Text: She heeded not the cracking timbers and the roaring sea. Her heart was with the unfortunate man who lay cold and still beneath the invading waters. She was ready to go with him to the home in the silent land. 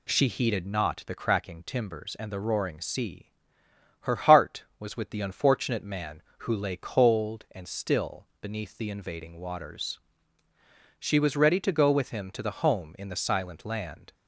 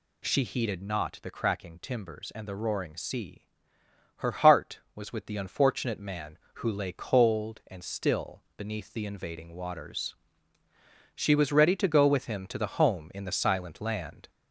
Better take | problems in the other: first | gets louder; slight; throughout; 2.5 dB

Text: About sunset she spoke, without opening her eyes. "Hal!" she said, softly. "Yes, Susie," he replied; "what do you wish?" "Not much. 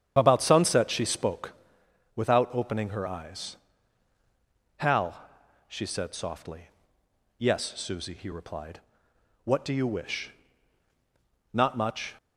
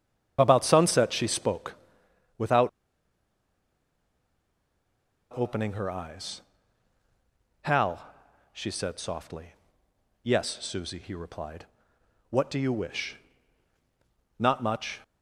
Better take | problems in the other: first | starts louder than the rest; strong; until 1.4 s; 9 dB; strong in the first // pauses between "without" and "opening"; strong; at 2.6 s; 2.6 s long

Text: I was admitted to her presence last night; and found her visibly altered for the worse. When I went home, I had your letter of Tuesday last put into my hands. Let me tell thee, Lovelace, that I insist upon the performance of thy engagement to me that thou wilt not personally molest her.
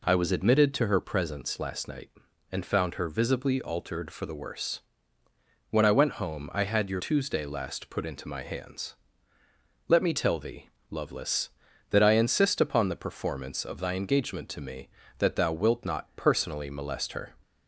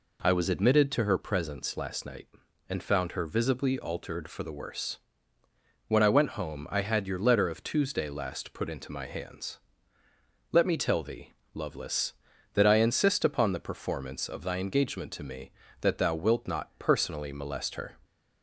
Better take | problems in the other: second | skips "letter of"; at 6.9 s

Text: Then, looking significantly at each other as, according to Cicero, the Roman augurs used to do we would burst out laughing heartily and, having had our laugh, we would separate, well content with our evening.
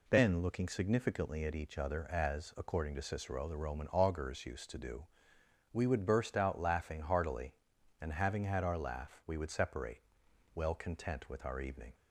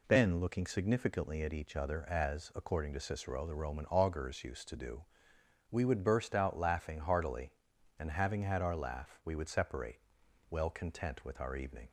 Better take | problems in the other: neither | pauses between "do" and "we"; noticeable; the same in both

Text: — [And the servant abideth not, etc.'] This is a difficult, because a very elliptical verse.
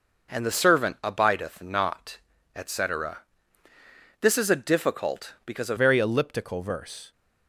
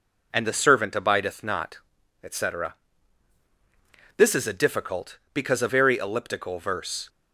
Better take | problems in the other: second | changes voice at "very"; from 5.7 s on; 1.4 s long

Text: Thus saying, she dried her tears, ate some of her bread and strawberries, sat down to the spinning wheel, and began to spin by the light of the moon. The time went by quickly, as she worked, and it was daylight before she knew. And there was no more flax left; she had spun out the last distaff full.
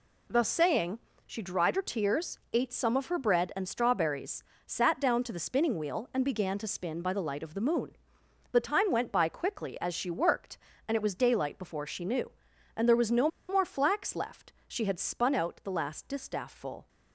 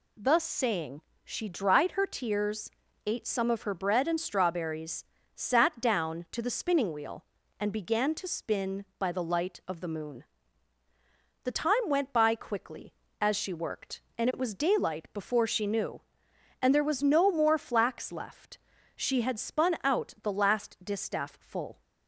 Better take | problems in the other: second | pauses between "no" and "more"; slight; at 13.2 s; 0.21 s long

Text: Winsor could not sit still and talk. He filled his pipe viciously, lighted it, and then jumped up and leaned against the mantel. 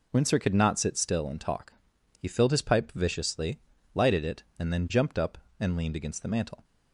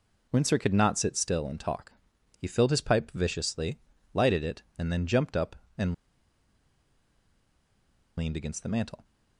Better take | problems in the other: first | pauses between "and" and "leaned"; strong; at 5.9 s; 2.2 s long

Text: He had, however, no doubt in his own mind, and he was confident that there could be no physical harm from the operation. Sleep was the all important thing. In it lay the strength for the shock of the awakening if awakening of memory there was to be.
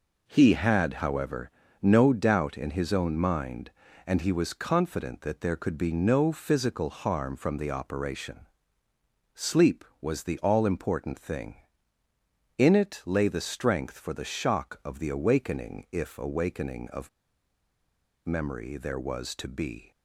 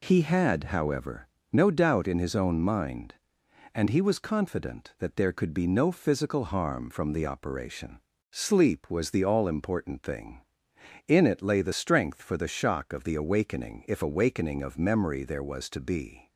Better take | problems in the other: second | pauses between "of" and "memory"; at 17.0 s; 1.1 s long

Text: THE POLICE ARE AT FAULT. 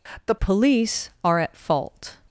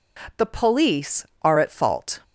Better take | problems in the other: second | changes voice at "POLICE"; from 0.3 s on; 1.8 s long

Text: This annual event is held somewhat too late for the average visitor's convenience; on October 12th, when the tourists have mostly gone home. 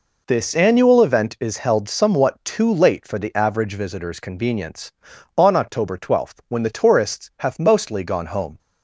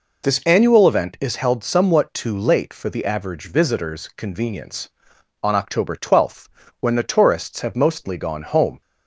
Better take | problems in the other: neither | none

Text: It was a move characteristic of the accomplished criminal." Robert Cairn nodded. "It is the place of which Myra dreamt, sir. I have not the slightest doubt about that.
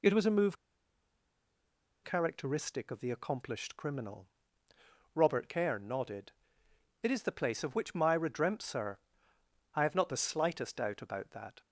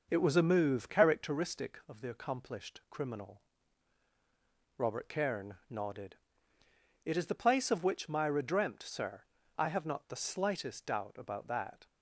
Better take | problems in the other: second | pauses between "move" and "characteristic"; strong; at 0.5 s; 1.4 s long

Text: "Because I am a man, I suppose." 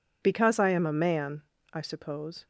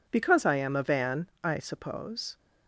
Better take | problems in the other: first | says "van" for "man"; at 0.8 s

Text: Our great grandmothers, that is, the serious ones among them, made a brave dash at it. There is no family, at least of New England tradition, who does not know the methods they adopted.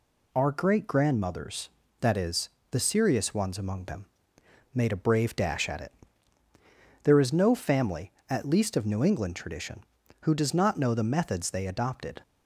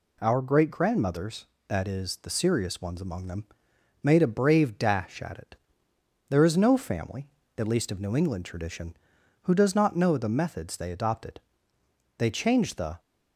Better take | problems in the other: first | goes on to say "They changed the"; noticeable; from 12.1 s on; 0.82 s long

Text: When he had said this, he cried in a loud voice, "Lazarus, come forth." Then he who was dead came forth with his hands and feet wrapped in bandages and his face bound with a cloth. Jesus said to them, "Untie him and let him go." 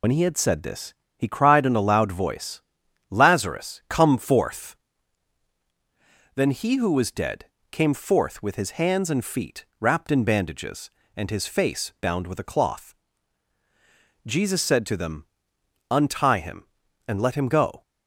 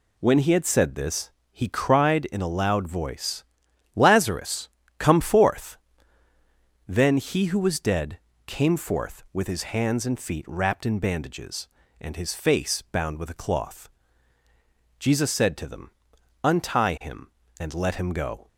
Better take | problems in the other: second | loses the start of "When"; at 0.0 s; 70 ms // pauses between "dead" and "came"; slight; at 7.4 s; 0.26 s long; slight in the second // pauses between "feet" and "wrapped"; slight; at 9.6 s; 0.16 s long

